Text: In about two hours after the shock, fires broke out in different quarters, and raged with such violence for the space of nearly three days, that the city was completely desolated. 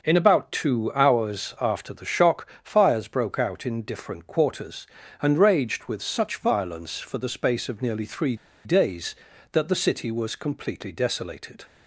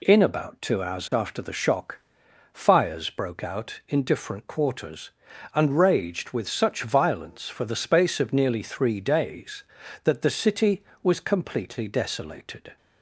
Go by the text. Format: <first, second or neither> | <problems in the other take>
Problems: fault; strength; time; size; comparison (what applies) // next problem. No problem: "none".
second | pauses between "three" and "days"; slight; at 8.3 s; 0.30 s long